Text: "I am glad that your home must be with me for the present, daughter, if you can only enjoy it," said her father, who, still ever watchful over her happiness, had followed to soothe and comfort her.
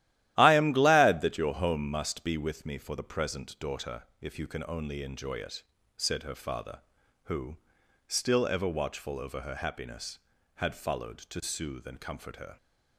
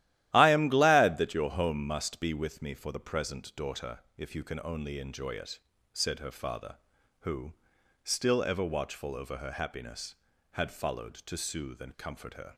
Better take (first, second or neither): neither